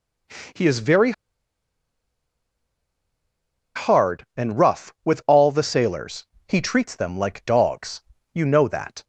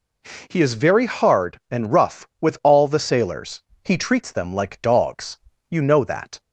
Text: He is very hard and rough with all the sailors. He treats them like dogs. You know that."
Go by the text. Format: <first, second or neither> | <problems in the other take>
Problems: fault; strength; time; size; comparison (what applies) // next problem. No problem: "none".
second | pauses between "very" and "hard"; strong; at 1.1 s; 2.6 s long